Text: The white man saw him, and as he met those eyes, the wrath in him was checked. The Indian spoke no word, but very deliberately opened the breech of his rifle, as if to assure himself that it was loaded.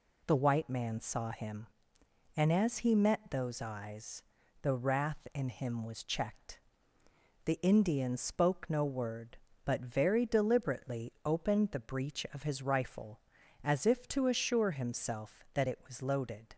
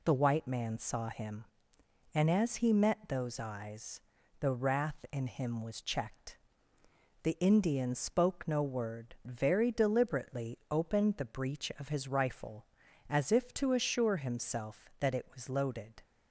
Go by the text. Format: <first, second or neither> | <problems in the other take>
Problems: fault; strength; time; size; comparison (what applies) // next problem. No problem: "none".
first | skips "but"; at 9.1 s